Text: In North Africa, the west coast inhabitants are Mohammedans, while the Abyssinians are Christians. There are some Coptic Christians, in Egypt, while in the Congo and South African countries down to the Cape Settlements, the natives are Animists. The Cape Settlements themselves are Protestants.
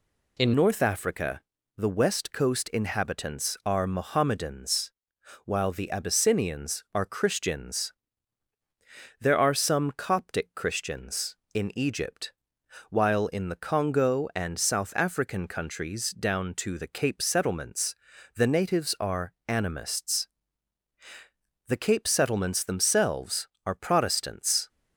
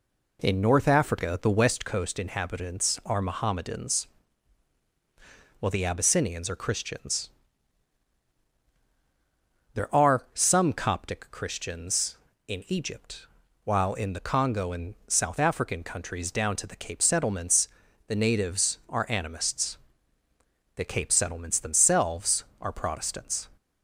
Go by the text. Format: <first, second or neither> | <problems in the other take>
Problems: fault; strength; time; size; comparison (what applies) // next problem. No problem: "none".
second | changes voice at "North"; from 0.5 s on; 24.1 s long // pauses between "are" and "Animists"; slight; at 19.3 s; 0.16 s long